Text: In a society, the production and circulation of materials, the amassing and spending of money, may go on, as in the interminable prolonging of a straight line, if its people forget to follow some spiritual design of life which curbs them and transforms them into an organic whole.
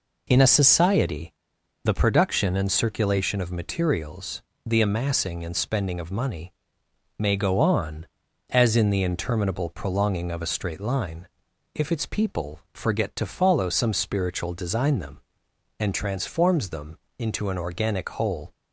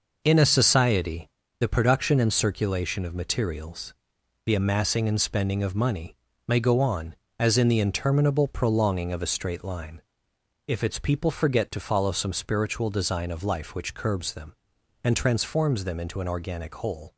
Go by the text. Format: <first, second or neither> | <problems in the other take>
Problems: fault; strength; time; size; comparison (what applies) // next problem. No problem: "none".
second | skips "of life which curbs"; at 14.9 s // pauses between "them" and "into"; slight; at 16.9 s; 0.20 s long